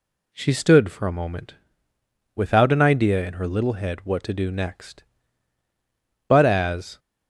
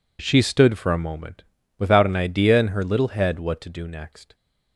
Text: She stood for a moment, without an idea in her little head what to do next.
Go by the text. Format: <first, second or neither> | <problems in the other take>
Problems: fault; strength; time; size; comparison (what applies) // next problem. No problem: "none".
second | goes on to say "But as"; noticeable; from 6.2 s on; 0.72 s long